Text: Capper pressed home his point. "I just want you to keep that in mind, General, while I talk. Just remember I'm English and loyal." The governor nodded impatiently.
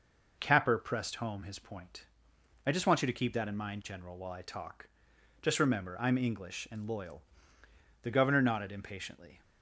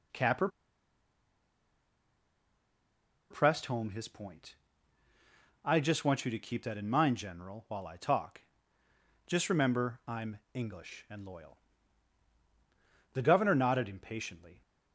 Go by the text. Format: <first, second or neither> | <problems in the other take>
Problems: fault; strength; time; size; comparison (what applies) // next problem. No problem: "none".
first | pauses between "Capper" and "pressed"; strong; at 0.4 s; 2.8 s long // pauses between "I'm" and "English"; slight; at 10.3 s; 0.16 s long